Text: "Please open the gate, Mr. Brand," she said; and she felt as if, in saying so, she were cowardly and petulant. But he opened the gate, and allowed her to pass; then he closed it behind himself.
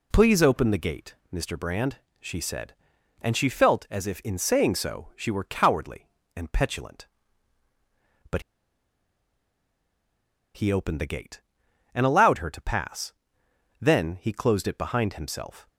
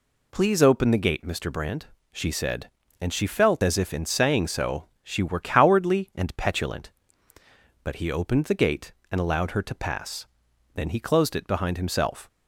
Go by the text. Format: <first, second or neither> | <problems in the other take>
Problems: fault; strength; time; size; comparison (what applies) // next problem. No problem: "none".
second | pauses between "But" and "he"; strong; at 8.4 s; 2.1 s long